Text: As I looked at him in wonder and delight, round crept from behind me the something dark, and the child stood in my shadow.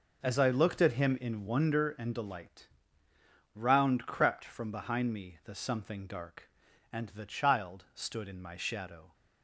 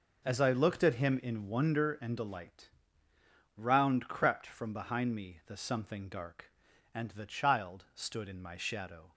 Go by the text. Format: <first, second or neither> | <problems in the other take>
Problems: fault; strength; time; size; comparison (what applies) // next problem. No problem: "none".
neither | none